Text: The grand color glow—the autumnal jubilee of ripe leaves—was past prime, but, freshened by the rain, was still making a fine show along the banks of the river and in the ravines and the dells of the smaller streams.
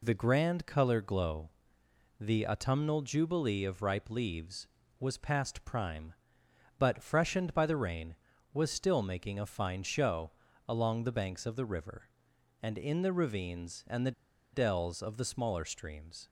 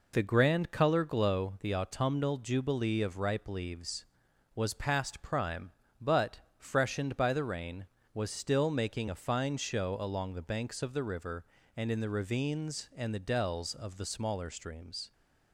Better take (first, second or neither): second